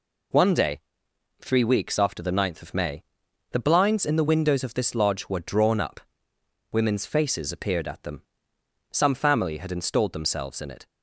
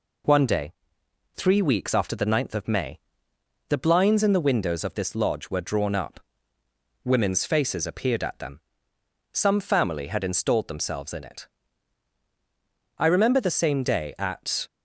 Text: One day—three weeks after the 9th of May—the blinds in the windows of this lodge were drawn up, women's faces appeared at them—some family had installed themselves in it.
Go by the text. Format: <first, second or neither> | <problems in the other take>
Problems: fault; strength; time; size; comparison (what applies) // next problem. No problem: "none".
first | goes on to say "I remember the same day at"; strong; from 12.9 s on; 1.7 s long